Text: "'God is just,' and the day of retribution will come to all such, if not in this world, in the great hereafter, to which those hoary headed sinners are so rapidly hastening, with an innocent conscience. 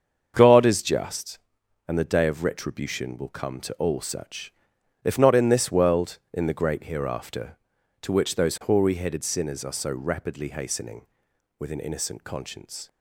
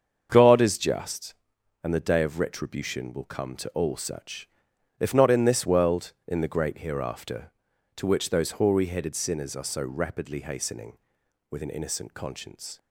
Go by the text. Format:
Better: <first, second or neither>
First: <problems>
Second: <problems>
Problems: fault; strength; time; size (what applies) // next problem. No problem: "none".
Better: neither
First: starts louder than the rest; until 1.3 s; 7 dB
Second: starts louder than the rest; until 1.3 s; 7 dB